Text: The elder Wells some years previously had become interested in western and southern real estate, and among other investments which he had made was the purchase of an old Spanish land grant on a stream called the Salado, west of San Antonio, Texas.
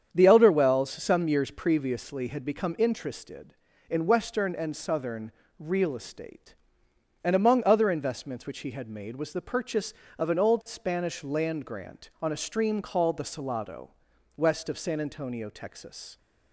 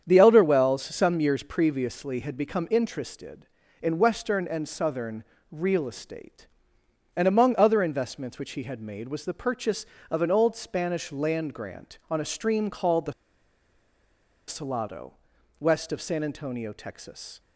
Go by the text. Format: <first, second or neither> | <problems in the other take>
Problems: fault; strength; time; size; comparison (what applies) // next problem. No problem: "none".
first | starts louder than the rest; strong; until 1.0 s; 8 dB; strong in the first // pauses between "southern" and "real"; slight; at 5.2 s; 0.26 s long; slight in the first // pauses between "the" and "Salado"; strong; at 13.1 s; 1.3 s long